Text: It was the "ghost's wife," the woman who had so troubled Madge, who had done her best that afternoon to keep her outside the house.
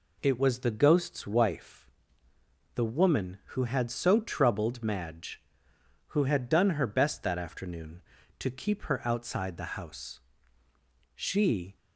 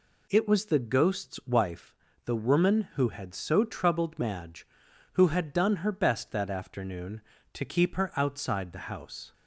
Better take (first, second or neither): second